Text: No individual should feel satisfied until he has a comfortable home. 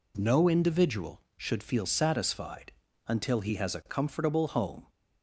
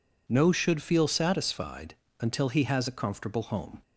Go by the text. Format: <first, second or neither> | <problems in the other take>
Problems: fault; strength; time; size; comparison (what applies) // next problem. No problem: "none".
first | skips "individual"; at 0.5 s // pauses between "satisfied" and "until"; slight; at 1.9 s; 0.24 s long; slight in the first